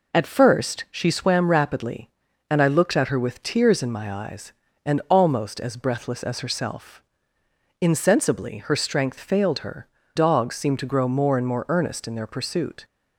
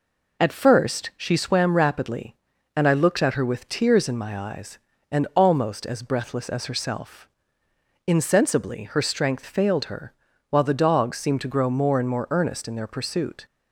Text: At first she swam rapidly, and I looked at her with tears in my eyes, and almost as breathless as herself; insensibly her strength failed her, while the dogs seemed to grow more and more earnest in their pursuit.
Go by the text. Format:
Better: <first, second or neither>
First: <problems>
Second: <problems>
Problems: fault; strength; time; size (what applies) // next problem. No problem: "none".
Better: second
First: skips "while the"; at 10.0 s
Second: none